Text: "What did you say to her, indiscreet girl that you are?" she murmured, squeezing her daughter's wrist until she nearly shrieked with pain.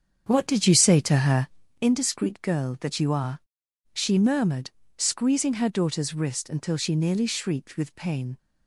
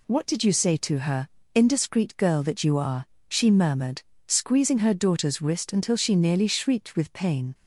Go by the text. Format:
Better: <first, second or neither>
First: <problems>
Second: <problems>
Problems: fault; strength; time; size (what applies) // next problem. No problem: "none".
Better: second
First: starts louder than the rest; strong; until 1.7 s; 7.5 dB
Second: none